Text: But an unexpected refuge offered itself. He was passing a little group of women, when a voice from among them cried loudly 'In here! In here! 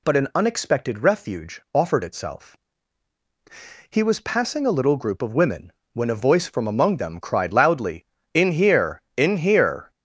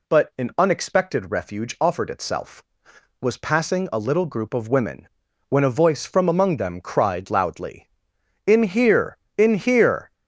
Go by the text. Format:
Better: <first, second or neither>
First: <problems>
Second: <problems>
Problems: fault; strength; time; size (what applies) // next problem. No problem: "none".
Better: first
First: none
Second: skips "He"; at 2.9 s